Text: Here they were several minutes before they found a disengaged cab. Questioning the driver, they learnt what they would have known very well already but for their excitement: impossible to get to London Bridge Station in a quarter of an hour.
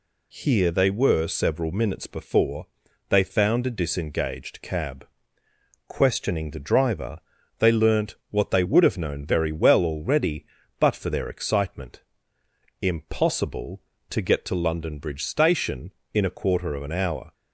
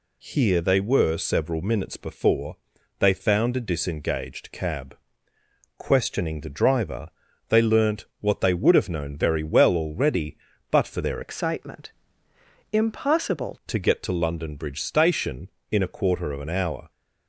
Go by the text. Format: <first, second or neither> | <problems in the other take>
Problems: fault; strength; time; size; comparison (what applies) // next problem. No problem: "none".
first | pauses between "before" and "they"; at 2.5 s; 0.44 s long; also in the first // changes voice from "excitement" to "impossible"; from 11.2 to 13.5 s; 2.3 s long